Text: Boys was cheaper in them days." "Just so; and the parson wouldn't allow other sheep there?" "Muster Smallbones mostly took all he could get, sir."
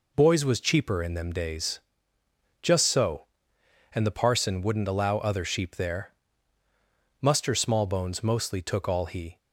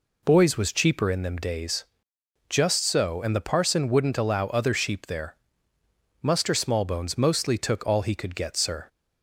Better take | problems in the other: second | stops before "could get sir"; at 9.3 s

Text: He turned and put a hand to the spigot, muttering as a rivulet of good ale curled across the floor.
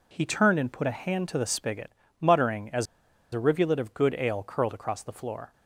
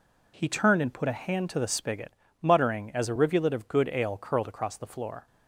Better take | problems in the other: second | pauses between "as" and "a"; noticeable; at 2.8 s; 0.46 s long

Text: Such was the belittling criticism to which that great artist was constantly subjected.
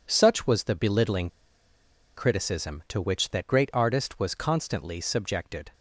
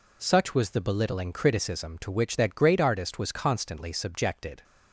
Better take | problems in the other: second | pauses between "belittling" and "criticism"; noticeable; at 1.2 s; 0.88 s long

